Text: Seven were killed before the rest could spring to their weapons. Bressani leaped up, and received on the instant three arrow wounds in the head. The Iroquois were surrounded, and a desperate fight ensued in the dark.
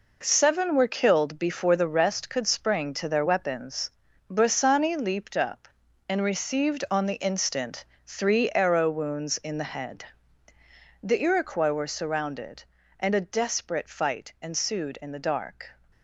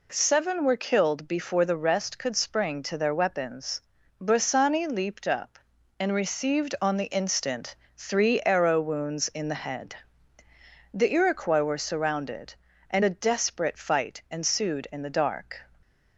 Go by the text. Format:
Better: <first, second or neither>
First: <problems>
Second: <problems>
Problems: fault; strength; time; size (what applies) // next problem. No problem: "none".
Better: second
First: gets quieter; strong; throughout; 8.5 dB // pauses between "instant" and "three"; slight; at 7.8 s; 0.20 s long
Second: pauses between "instant" and "three"; slight; at 7.7 s; 0.20 s long